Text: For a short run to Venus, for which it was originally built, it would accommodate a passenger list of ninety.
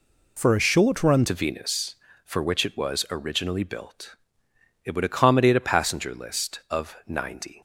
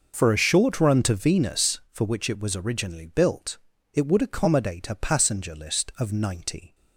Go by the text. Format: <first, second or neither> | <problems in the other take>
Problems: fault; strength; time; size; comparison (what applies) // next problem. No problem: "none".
second | changes voice at "to"; from 1.2 s on; 6.4 s long